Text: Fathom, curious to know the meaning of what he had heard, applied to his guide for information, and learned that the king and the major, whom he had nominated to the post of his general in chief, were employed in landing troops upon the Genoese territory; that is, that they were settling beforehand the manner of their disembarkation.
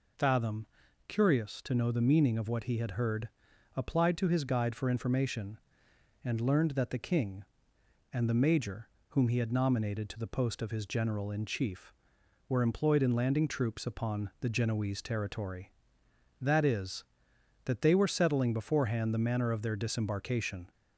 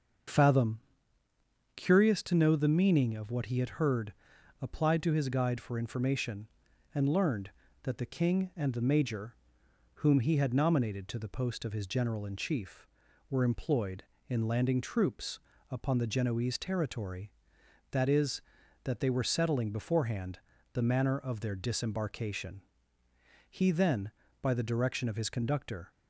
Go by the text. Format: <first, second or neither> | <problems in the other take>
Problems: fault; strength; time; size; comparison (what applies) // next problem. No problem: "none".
first | starts louder than the rest; until 2.2 s; 6.5 dB // pauses between "troops" and "upon"; slight; at 15.3 s; 0.32 s long // pauses between "beforehand" and "the"; slight; at 20.4 s; 0.34 s long // goes on to say "He then by the direction of his conductor"; strong; from 23.4 s on; 2.4 s long